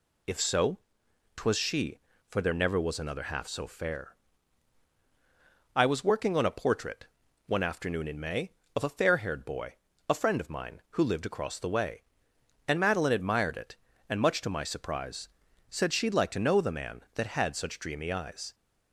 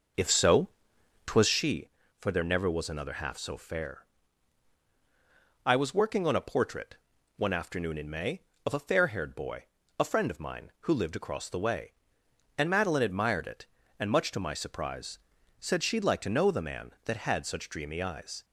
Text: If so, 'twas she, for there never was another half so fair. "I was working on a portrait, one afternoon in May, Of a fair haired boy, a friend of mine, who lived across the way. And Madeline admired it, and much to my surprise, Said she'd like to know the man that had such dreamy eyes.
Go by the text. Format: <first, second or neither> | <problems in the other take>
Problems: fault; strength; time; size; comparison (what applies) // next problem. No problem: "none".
first | starts louder than the rest; noticeable; until 1.7 s; 5.5 dB